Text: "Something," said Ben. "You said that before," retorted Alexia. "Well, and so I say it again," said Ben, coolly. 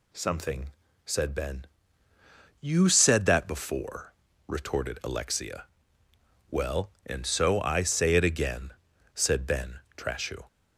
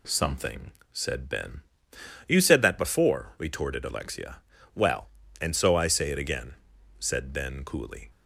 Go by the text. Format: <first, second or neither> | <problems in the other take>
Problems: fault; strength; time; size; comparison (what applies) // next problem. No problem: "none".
second | says "trashu" for "coolly"; at 9.9 s